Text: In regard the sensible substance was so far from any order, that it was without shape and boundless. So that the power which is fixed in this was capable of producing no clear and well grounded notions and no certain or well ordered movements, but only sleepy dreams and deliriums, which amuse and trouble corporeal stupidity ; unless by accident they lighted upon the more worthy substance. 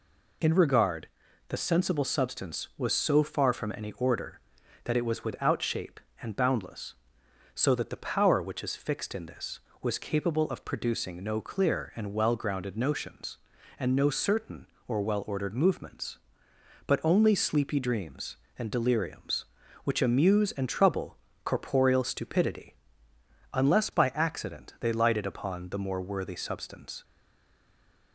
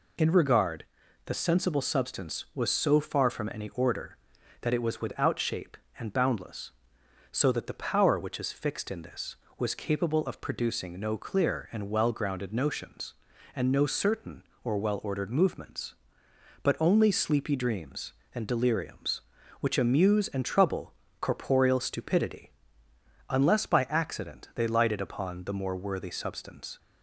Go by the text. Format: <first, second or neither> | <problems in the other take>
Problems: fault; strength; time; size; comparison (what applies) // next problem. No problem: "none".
second | pauses between "regard" and "the"; at 1.0 s; 0.40 s long; also in the second // pauses between "trouble" and "corporeal"; slight; at 21.1 s; 0.30 s long; slight in the second // stays silent after the last word; from 27.0 s on; 1.1 s long